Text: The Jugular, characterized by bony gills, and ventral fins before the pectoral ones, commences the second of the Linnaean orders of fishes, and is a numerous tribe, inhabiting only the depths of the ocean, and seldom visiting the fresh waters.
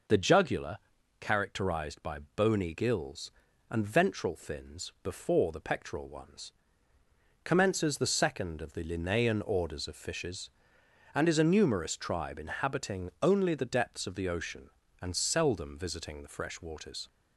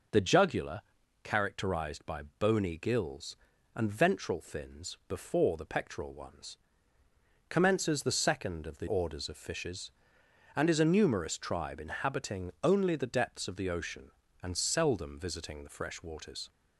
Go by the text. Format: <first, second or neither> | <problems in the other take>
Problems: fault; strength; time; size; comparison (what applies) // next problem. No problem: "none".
first | skips "Linnaean"; at 8.8 s